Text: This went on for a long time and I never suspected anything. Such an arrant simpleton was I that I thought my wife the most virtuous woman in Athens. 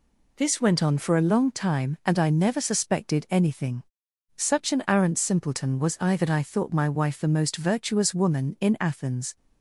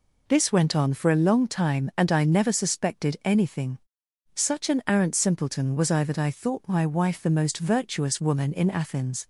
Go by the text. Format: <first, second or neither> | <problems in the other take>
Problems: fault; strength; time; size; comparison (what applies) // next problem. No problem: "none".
neither | none